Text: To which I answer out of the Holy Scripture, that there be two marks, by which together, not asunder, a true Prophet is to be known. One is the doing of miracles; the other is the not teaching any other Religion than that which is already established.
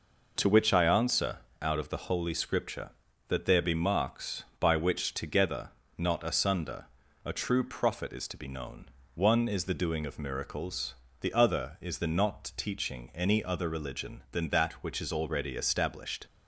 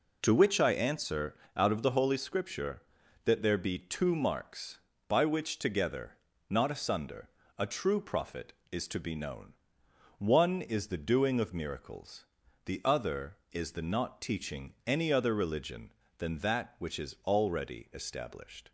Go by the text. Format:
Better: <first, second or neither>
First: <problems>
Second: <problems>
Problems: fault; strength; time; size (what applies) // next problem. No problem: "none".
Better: second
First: pauses between "answer" and "out"; slight; at 1.3 s; 0.24 s long // skips "two"; at 3.7 s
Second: pauses between "answer" and "out"; slight; at 1.3 s; 0.18 s long